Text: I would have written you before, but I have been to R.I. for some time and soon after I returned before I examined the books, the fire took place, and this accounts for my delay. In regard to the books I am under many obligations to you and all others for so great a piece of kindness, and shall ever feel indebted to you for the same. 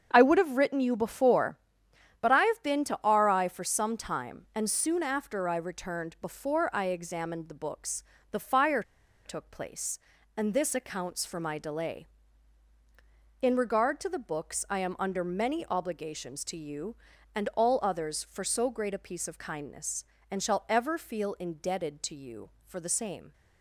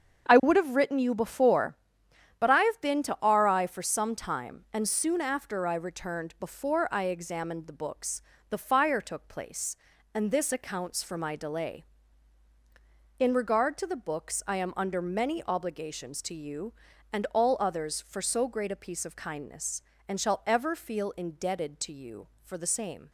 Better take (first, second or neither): second